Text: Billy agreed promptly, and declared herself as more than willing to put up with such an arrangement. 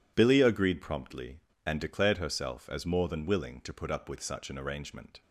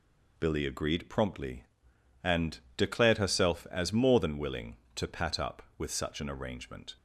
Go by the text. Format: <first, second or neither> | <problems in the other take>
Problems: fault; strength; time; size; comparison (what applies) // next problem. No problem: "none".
first | pauses between "and" and "declared"; slight; at 2.6 s; 0.16 s long // says "pat" for "put"; at 5.0 s